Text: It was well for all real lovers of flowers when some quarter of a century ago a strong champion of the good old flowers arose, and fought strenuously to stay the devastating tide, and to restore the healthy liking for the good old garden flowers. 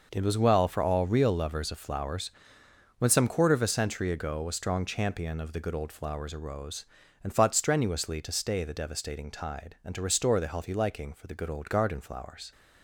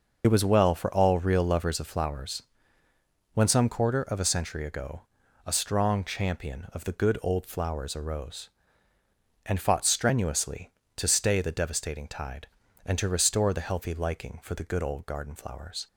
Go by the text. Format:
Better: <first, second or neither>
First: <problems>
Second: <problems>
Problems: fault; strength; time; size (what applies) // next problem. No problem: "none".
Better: first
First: pauses between "flowers" and "when"; noticeable; at 2.3 s; 0.66 s long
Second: loses the start of "It"; at 0.2 s; 40 ms // pauses between "flowers" and "when"; noticeable; at 2.4 s; 0.90 s long // pauses between "ago" and "a"; at 5.0 s; 0.44 s long